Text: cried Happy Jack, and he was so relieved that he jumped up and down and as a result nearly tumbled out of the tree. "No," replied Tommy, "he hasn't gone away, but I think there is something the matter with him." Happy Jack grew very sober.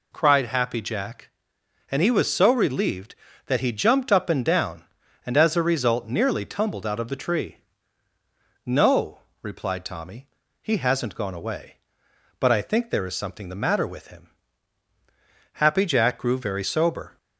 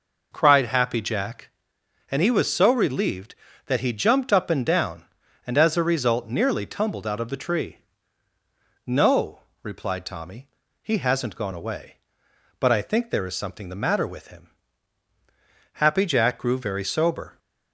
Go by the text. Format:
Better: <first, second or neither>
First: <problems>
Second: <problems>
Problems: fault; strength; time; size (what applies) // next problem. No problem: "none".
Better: first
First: none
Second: starts louder than the rest; noticeable; until 1.7 s; 5 dB